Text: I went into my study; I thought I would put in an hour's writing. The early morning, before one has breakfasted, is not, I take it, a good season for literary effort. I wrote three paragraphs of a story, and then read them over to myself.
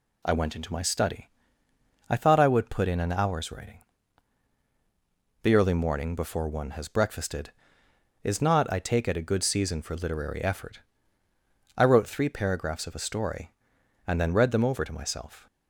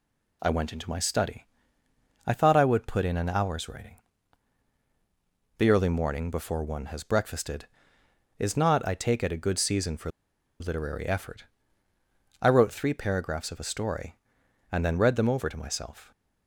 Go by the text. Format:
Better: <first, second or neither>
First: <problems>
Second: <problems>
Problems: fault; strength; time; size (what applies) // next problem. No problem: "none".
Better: first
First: none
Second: pauses between "for" and "literary"; noticeable; at 10.0 s; 0.50 s long